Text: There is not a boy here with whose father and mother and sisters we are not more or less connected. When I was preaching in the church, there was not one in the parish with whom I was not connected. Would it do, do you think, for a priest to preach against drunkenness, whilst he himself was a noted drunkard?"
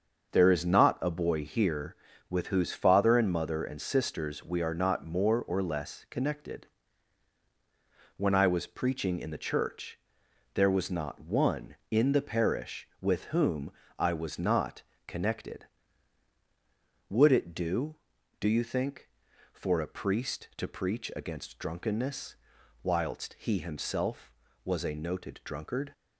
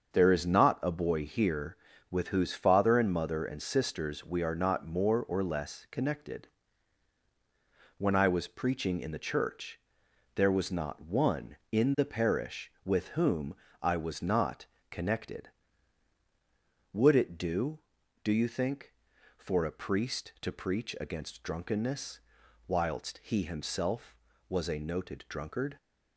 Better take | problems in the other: neither | starts louder than the rest; the same in both // pauses between "whom" and "I"; slight; the same in both // pauses between "not" and "connected"; slight; the same in both

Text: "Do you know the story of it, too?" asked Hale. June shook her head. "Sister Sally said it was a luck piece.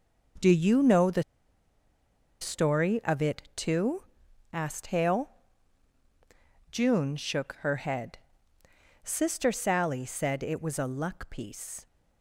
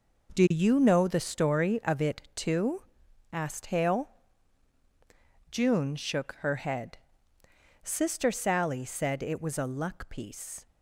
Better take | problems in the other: second | pauses between "the" and "story"; at 1.2 s; 1.1 s long

